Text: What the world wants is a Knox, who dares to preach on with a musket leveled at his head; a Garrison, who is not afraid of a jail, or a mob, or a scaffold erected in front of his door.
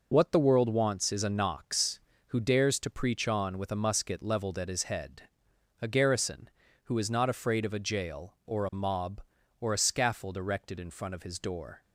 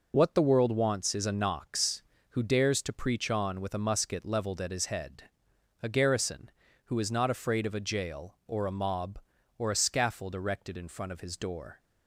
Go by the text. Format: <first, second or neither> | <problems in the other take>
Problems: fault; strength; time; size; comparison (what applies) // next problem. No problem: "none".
neither | none